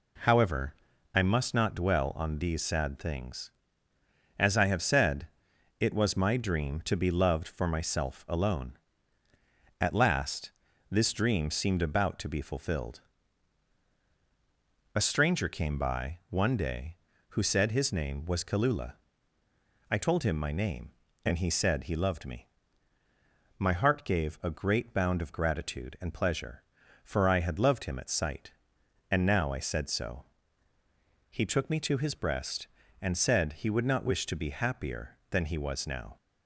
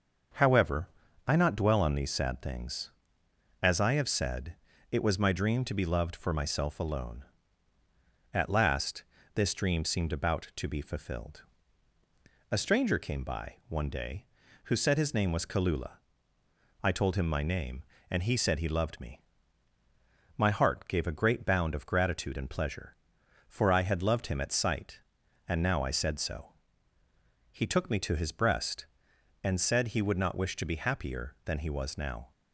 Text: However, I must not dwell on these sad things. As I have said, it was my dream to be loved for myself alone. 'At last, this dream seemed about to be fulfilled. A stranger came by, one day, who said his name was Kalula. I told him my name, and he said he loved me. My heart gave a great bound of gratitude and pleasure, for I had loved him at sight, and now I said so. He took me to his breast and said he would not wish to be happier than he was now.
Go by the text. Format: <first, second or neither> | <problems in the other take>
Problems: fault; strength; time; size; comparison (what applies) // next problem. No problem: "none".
first | starts louder than the rest; until 1.7 s; 6.5 dB // skips "must"; at 1.3 s